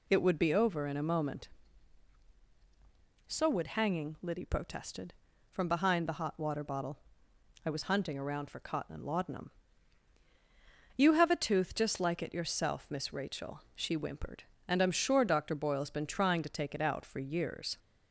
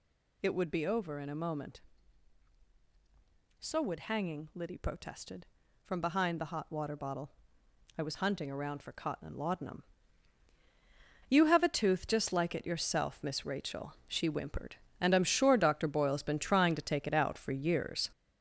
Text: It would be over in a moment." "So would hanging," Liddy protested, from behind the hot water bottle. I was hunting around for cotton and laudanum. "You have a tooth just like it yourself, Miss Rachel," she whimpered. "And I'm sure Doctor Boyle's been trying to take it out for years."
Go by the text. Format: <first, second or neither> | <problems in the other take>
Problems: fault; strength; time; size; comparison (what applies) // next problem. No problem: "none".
first | gets louder; throughout; 6.5 dB